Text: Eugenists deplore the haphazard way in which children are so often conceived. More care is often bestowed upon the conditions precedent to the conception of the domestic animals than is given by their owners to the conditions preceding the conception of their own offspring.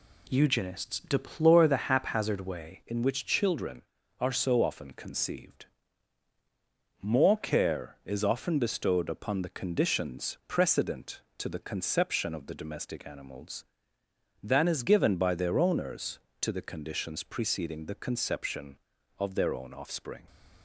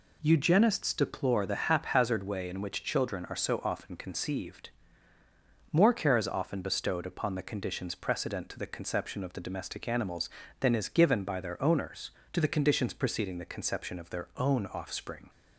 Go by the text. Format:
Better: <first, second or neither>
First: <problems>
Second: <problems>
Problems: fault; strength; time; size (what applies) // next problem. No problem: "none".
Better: second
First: changes voice at "in"; from 2.8 s on; 17.4 s long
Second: none